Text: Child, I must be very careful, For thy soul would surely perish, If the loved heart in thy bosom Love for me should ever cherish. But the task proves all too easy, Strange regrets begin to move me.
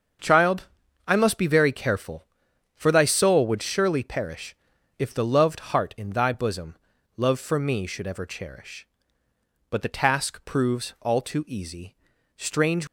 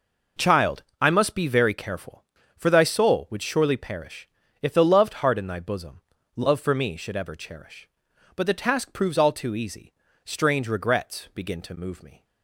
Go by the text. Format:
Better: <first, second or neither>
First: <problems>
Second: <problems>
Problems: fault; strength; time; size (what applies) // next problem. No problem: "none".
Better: second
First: starts louder than the rest; until 1.6 s; 7 dB // pauses between "bosom" and "Love"; at 6.7 s; 0.40 s long // stops before "regrets begin to move me"; at 12.8 s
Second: pauses between "bosom" and "Love"; slight; at 6.0 s; 0.34 s long